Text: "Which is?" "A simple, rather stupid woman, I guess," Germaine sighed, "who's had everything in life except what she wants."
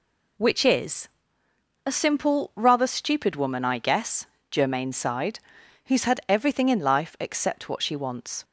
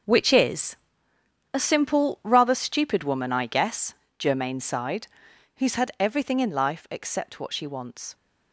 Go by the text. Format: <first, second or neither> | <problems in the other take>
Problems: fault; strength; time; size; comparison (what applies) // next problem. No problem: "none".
first | gets quieter; strong; throughout; 11 dB